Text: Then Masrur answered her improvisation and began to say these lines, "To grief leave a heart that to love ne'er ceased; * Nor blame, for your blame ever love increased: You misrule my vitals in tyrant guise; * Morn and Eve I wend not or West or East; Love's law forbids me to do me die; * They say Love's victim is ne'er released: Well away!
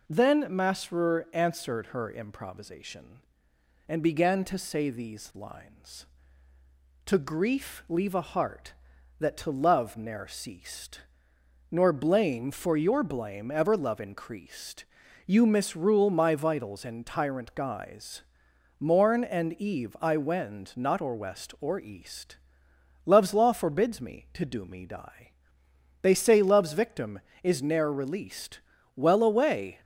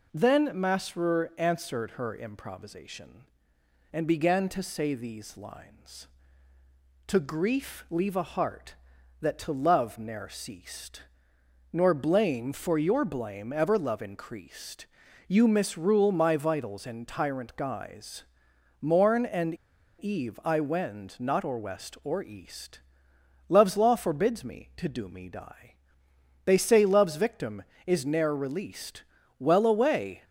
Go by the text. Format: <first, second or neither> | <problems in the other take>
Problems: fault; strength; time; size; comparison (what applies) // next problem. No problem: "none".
first | pauses between "and" and "Eve"; noticeable; at 19.5 s; 0.49 s long